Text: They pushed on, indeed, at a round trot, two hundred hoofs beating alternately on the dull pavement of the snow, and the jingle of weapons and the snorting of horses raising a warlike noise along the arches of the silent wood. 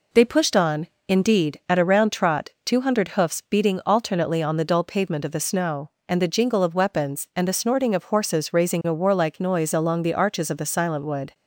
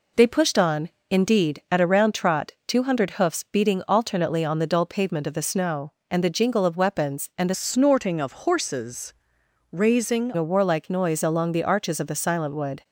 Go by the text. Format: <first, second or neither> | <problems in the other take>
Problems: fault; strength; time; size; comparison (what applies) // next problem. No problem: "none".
first | changes voice from "snorting" to "raising"; from 7.5 to 10.3 s; 2.8 s long // pauses between "horses" and "raising"; noticeable; at 9.1 s; 0.58 s long